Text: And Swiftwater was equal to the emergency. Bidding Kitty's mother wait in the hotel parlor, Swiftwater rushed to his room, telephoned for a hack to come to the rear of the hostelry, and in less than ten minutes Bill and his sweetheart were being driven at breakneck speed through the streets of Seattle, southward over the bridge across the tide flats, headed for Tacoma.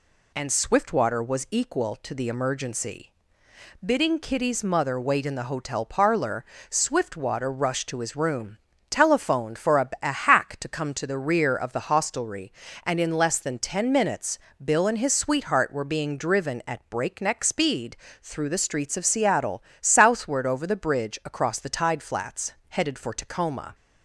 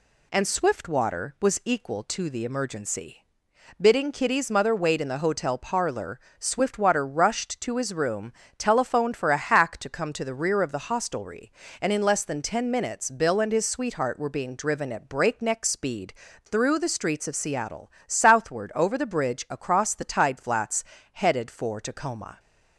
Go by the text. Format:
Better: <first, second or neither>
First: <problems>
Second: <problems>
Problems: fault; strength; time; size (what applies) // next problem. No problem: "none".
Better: second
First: says "a" twice; at 10.0 s // pauses between "minutes" and "Bill"; slight; at 14.3 s; 0.24 s long // pauses between "speed" and "through"; slight; at 17.9 s; 0.26 s long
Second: pauses between "speed" and "through"; slight; at 16.1 s; 0.32 s long